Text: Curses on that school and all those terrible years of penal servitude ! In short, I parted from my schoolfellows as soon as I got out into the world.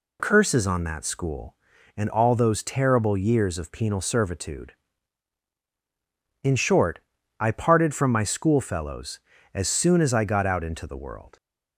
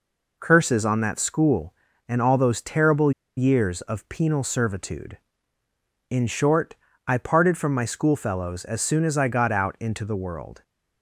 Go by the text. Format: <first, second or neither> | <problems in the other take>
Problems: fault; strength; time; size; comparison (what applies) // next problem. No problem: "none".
first | pauses between "terrible" and "years"; slight; at 3.1 s; 0.26 s long